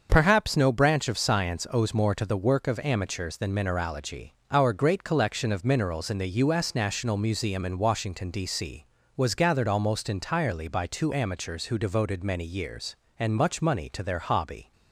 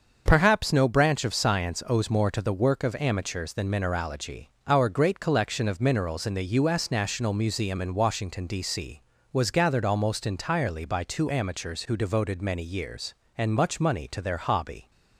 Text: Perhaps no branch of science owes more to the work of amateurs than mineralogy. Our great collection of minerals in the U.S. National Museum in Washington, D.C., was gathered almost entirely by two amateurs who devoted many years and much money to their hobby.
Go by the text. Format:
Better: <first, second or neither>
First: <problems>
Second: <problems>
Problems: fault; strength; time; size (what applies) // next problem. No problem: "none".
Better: neither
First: starts louder than the rest; until 1.1 s; 6.5 dB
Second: starts louder than the rest; until 1.2 s; 6.5 dB